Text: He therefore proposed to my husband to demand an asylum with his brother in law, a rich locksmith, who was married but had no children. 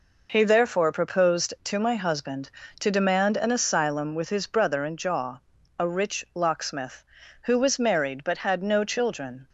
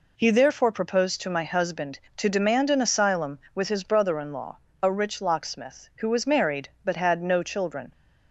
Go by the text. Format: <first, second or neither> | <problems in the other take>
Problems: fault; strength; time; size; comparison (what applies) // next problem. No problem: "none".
second | says "jaw" for "law"; at 4.9 s